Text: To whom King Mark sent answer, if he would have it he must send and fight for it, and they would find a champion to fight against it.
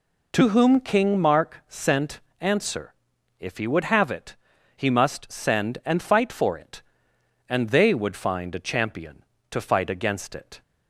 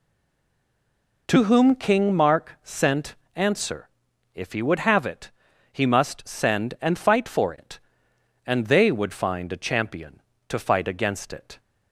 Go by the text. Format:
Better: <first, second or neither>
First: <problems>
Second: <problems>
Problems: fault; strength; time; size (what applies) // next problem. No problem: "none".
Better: first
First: pauses between "sent" and "answer"; slight; at 2.1 s; 0.22 s long // pauses between "it" and "he"; at 4.3 s; 0.41 s long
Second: stays silent before the first word; noticeable; until 1.2 s; 1.2 s long // pauses between "sent" and "answer"; slight; at 3.1 s; 0.22 s long // pauses between "it" and "he"; at 5.3 s; 0.42 s long